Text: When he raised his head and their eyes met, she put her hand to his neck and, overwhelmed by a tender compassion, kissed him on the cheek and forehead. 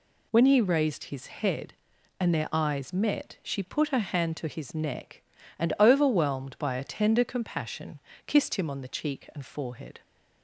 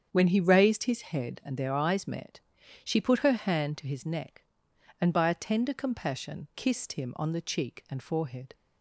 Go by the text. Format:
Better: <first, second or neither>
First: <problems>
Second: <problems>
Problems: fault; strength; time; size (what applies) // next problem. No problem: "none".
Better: first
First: none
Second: starts louder than the rest; strong; until 1.1 s; 8 dB // skips "overwhelmed"; at 5.1 s